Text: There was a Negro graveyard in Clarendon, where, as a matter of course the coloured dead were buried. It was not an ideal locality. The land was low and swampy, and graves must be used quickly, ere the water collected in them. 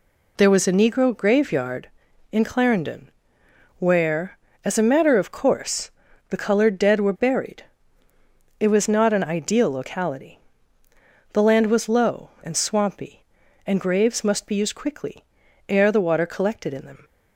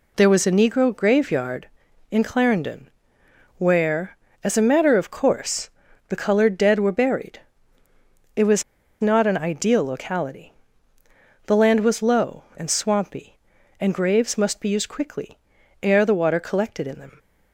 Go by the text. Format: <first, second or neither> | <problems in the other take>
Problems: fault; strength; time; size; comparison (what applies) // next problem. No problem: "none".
first | pauses between "course" and "the"; at 5.7 s; 0.38 s long; also in the first // pauses between "was" and "not"; at 8.6 s; 0.38 s long